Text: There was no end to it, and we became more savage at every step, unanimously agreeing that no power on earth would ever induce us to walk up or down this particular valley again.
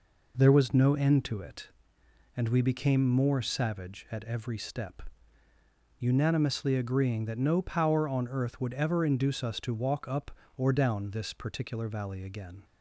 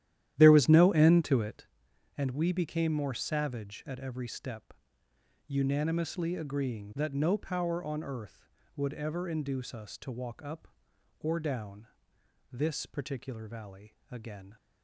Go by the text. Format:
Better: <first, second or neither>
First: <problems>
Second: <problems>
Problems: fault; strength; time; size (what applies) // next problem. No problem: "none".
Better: first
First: none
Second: starts louder than the rest; strong; until 1.7 s; 12 dB // pauses between "down" and "this"; noticeable; at 11.8 s; 0.64 s long // pauses between "valley" and "again"; slight; at 13.9 s; 0.18 s long